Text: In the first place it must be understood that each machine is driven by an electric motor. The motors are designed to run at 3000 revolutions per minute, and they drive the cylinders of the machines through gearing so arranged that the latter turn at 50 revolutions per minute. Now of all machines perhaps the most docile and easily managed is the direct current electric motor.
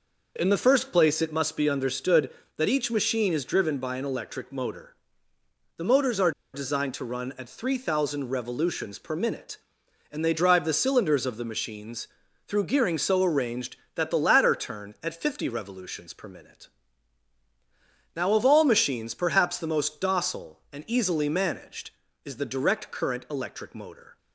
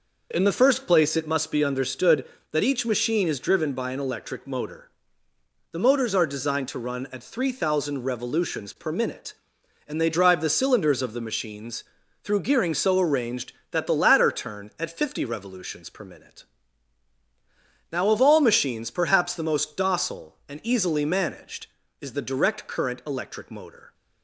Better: second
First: pauses between "are" and "designed"; slight; at 6.3 s; 0.23 s long // pauses between "machines" and "through"; at 12.0 s; 0.40 s long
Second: pauses between "machines" and "through"; at 11.8 s; 0.40 s long

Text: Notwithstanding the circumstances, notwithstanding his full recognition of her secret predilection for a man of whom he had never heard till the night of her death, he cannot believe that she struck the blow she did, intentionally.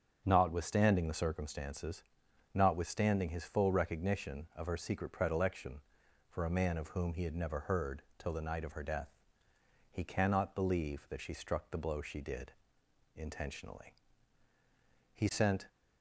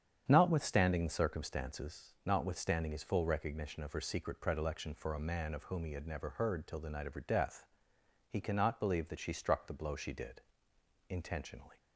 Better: second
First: starts louder than the rest; until 1.2 s; 7 dB // pauses between "heard" and "till"; slight; at 8.0 s; 0.16 s long // goes on to say "He sent"; from 15.1 s on; 0.53 s long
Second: starts louder than the rest; strong; until 1.2 s; 8.5 dB

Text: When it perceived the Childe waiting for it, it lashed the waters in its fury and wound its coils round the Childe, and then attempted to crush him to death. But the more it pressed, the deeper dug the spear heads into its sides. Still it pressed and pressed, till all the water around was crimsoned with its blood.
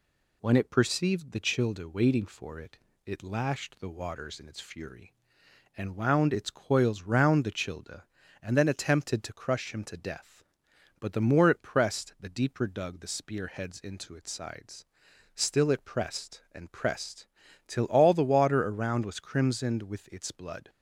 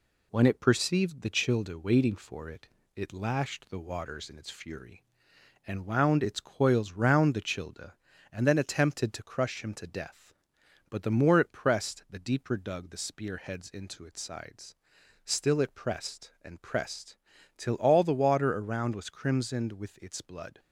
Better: first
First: none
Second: gets quieter; slight; throughout; 2.5 dB

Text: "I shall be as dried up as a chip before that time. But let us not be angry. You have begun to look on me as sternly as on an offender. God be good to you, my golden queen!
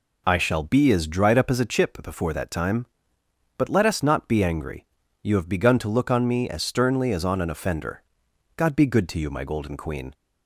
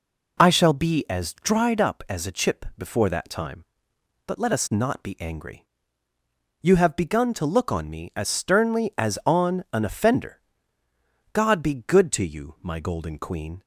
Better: neither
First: none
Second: none

